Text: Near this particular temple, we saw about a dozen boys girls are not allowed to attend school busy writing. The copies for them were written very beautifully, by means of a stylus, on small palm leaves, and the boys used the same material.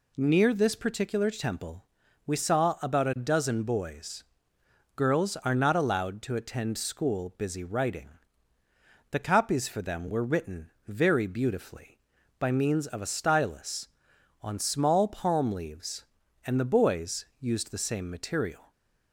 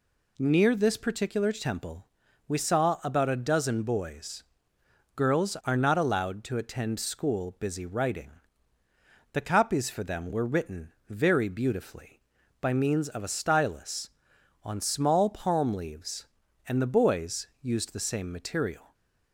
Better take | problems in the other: neither | pauses between "boys" and "girls"; noticeable; the same in both // pauses between "written" and "very"; slight; the same in both // pauses between "boys" and "used"; slight; the same in both

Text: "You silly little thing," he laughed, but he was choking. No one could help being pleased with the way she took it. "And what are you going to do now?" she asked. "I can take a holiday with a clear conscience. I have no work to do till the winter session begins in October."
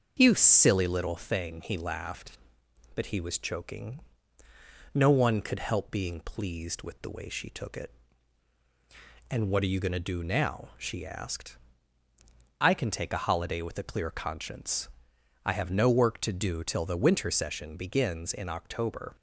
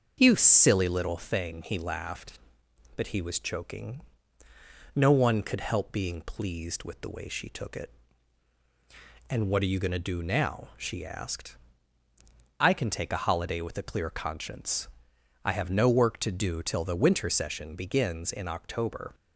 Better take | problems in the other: neither | starts louder than the rest; the same in both

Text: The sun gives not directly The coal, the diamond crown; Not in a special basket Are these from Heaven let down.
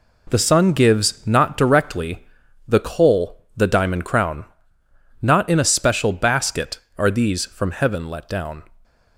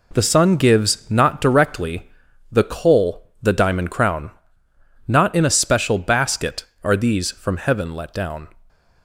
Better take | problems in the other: neither | pauses between "directly" and "The"; the same in both

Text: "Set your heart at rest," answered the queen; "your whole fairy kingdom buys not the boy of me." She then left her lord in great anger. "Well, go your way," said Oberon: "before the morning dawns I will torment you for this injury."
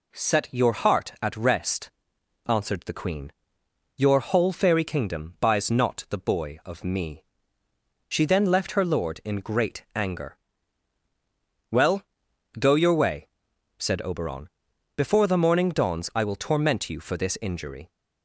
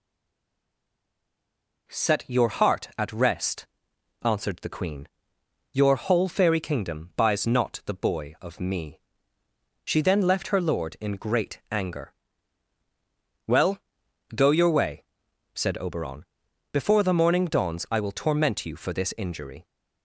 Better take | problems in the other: first | stays silent before the first word; noticeable; until 1.8 s; 1.8 s long

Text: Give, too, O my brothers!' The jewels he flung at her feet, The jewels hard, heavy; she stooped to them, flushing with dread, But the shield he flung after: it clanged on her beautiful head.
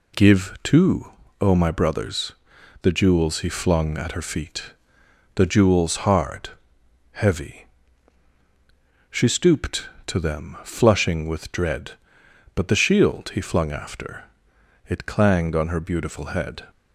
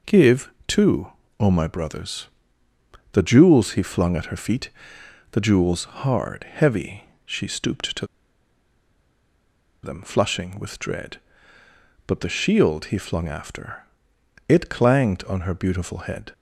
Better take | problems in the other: first | pauses between "to" and "them"; strong; at 8.0 s; 1.7 s long

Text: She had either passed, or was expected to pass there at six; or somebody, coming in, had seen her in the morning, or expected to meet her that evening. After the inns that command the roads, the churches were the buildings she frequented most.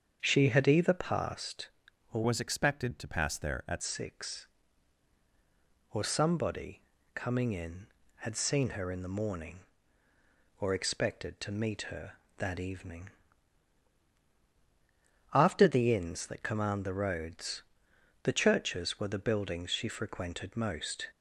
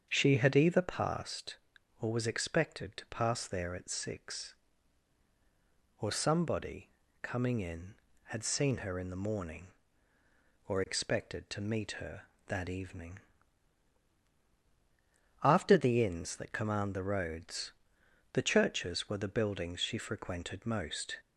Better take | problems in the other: second | starts louder than the rest; strong; until 1.2 s; 7.5 dB; strong in the second // changes voice from "was" to "at"; from 2.2 to 3.8 s; 1.6 s long

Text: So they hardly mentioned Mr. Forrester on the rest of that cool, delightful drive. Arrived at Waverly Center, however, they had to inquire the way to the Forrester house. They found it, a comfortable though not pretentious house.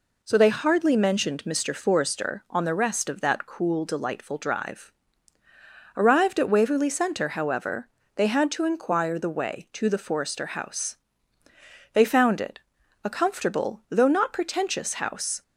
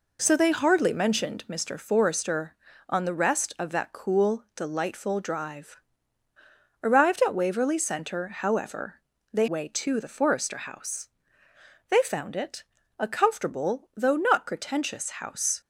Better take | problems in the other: first | skips "had to inquire the"; at 9.4 s

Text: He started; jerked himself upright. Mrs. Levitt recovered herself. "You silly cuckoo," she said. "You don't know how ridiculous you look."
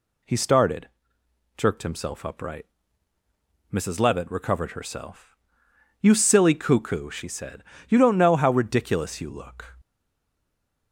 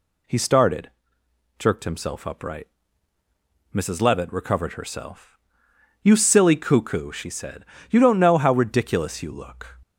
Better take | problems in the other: second | stays silent after the last word; from 9.8 s on; 1.1 s long

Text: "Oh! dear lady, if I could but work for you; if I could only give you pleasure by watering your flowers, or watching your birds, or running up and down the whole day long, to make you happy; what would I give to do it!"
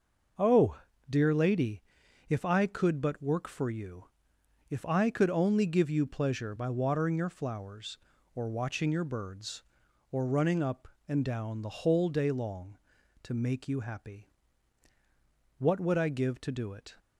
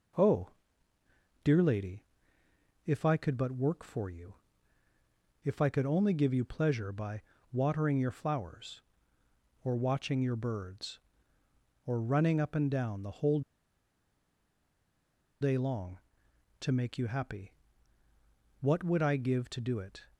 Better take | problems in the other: first | pauses between "by" and "watering"; slight; at 7.2 s; 0.30 s long // pauses between "whole" and "day"; strong; at 13.4 s; 2.0 s long

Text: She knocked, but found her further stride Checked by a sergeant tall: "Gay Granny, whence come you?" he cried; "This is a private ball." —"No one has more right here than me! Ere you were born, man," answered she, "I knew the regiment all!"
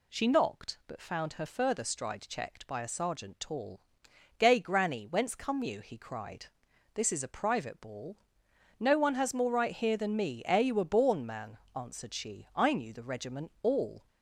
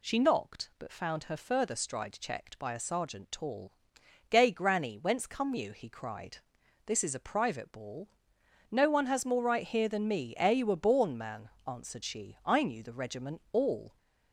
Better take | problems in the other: neither | none

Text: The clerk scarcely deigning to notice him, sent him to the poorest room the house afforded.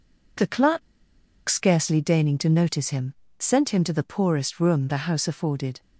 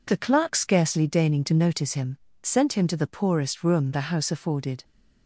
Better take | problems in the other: second | pauses between "clerk" and "scarcely"; noticeable; at 0.8 s; 0.66 s long

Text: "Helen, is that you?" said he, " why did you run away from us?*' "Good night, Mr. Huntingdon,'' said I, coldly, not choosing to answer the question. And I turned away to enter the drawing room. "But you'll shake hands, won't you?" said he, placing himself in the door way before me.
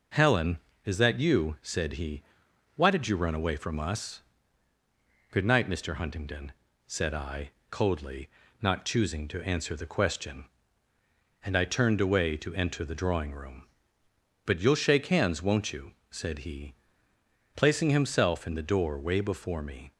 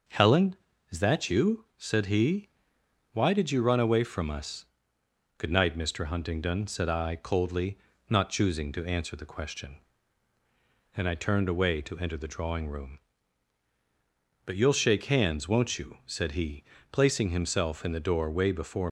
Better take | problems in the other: first | starts louder than the rest; noticeable; until 1.4 s; 6 dB // stops before "me"; at 18.8 s

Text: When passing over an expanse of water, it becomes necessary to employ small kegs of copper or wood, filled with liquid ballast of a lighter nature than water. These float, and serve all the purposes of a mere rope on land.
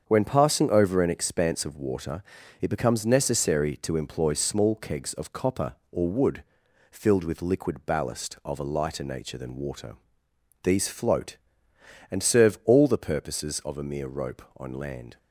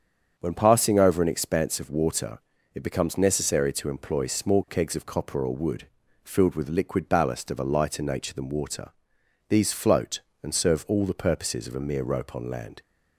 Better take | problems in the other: neither | starts louder than the rest; strong; the same in both

